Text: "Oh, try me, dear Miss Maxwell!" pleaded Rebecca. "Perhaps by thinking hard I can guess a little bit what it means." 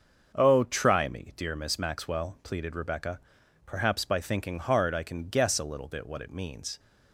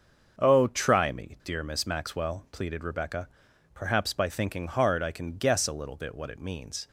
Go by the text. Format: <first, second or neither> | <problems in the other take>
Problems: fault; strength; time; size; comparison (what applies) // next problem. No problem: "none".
neither | starts louder than the rest; the same in both